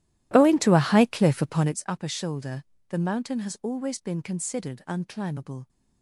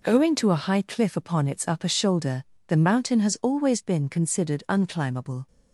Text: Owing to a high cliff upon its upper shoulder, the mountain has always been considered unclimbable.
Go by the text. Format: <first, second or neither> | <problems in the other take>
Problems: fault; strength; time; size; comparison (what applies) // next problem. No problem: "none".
second | starts louder than the rest; strong; until 1.8 s; 14.5 dB